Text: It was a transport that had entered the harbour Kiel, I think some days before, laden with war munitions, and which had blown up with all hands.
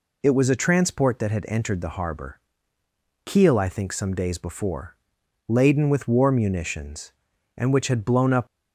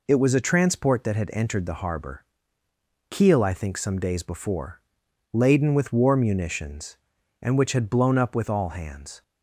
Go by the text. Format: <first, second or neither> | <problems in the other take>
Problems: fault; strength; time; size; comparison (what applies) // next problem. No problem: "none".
second | pauses between "harbour" and "Kiel"; noticeable; at 2.3 s; 0.86 s long; noticeable in the second // stops before "with all hands"; at 8.4 s